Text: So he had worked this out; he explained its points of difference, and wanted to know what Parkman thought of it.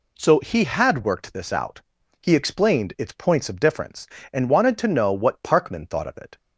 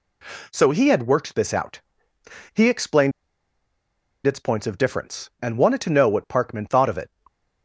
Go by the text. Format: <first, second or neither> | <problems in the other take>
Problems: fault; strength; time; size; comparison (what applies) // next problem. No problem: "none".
first | pauses between "explained" and "its"; at 3.1 s; 1.1 s long